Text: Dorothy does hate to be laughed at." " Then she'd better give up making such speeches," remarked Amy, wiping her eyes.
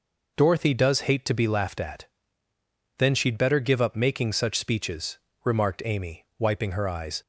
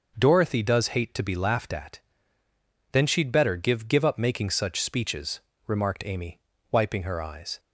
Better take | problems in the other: first | says "give" twice; at 3.8 s

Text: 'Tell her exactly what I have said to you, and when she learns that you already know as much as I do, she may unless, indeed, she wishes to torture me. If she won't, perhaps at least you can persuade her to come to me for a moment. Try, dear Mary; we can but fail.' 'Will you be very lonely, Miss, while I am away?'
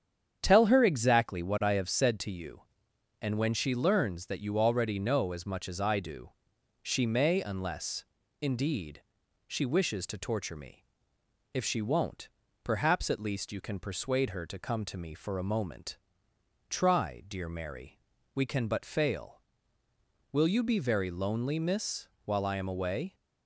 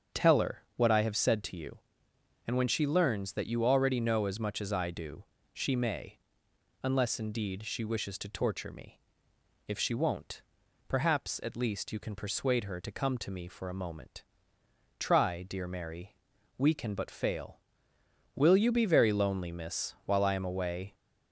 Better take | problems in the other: first | starts louder than the rest; strong; until 1.2 s; 7 dB; strong in the first // skips "exactly"; at 0.6 s // pauses between "may" and "unless"; noticeable; at 6.1 s; 0.66 s long

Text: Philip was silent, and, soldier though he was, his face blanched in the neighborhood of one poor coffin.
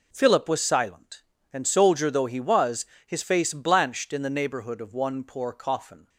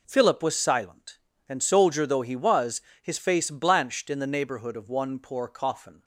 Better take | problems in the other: neither | none

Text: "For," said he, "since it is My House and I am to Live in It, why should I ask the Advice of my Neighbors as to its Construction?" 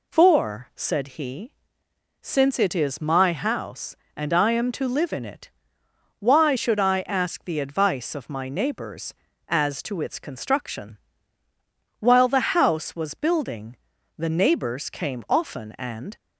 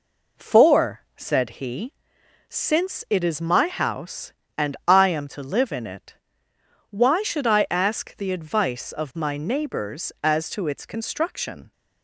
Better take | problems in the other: second | goes on to say "While the House was Building the Neighbors came often and"; strong; from 11.9 s on; 4.1 s long

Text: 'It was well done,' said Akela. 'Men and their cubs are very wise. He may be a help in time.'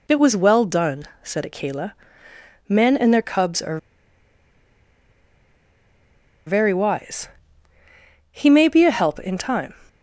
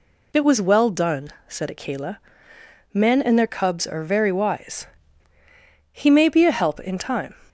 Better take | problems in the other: second | pauses between "are" and "very"; strong; at 3.7 s; 2.6 s long

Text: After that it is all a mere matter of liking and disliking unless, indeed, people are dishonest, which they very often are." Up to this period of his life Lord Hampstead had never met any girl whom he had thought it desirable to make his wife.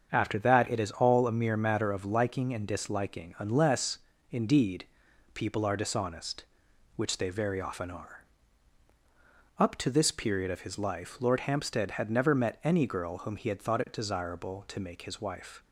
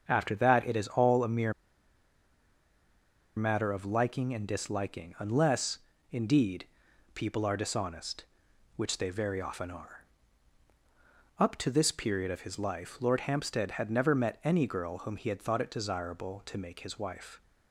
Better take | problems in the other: first | starts louder than the rest; until 1.0 s; 7 dB; also in the first // pauses between "mere" and "matter"; strong; at 1.5 s; 1.8 s long

